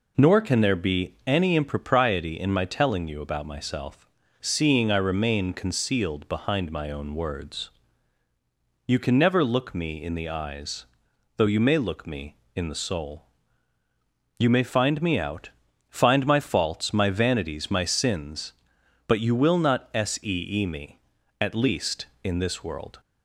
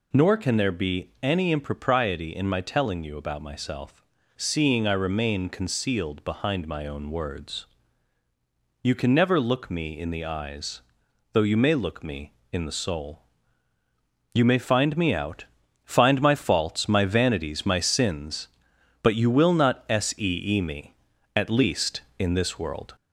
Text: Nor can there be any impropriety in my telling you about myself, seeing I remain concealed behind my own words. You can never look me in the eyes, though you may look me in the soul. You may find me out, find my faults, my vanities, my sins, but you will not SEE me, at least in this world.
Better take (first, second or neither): first